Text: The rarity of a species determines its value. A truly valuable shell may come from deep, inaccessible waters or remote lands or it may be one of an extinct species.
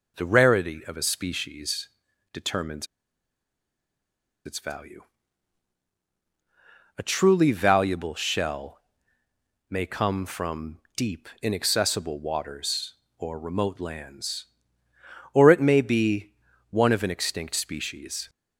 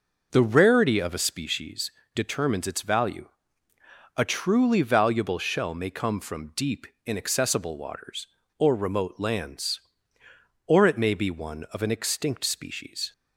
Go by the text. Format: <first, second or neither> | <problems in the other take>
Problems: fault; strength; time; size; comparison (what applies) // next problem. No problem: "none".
second | pauses between "species" and "determines"; at 1.8 s; 0.44 s long; slight in the second // pauses between "determines" and "its"; strong; at 2.8 s; 1.5 s long // pauses between "shell" and "may"; noticeable; at 8.7 s; 0.92 s long // pauses between "from" and "deep"; slight; at 10.7 s; 0.18 s long // pauses between "be" and "one"; at 16.3 s; 0.38 s long